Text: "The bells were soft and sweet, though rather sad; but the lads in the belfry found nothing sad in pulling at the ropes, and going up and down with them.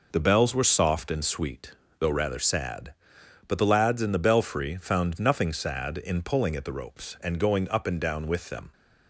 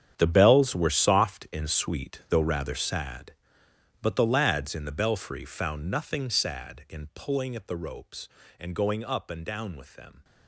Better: first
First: none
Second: gets quieter; strong; throughout; 16 dB

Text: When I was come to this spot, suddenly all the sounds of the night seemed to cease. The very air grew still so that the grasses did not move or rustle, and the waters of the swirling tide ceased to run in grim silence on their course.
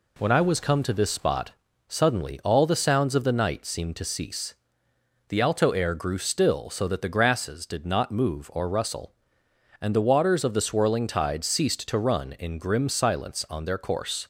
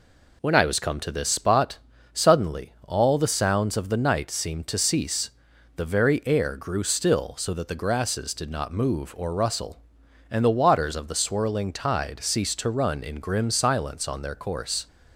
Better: second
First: says "alto" for "very"; at 5.4 s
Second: none

